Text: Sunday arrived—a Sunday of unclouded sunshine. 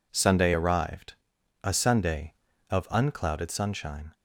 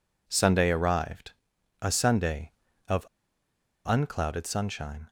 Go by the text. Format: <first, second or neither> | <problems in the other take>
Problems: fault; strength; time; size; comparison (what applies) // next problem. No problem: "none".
first | pauses between "of" and "unclouded"; noticeable; at 3.0 s; 0.79 s long